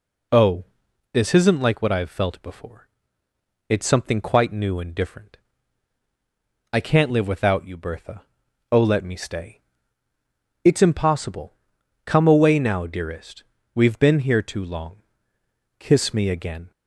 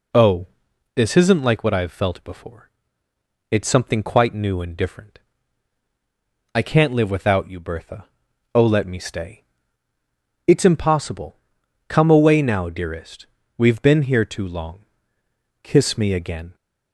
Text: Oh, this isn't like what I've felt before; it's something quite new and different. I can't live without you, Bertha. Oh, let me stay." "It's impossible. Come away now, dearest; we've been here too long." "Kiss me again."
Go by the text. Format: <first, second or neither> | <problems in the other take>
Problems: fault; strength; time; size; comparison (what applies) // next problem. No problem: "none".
neither | none